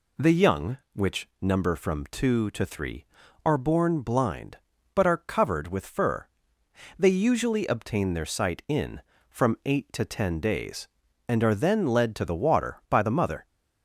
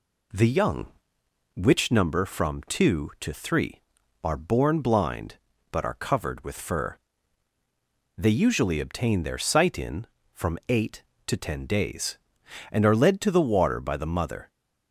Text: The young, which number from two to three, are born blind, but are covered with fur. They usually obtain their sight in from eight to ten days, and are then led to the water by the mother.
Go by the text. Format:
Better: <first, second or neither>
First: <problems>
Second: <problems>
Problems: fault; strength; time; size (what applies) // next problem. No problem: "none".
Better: first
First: none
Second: skips "then"; at 12.9 s